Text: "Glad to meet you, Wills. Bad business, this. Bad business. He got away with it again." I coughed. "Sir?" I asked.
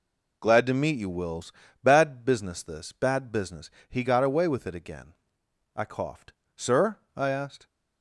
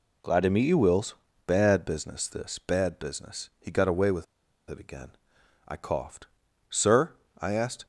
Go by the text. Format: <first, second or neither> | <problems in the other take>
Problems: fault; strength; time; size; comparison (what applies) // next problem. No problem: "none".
first | pauses between "with" and "it"; at 4.2 s; 0.45 s long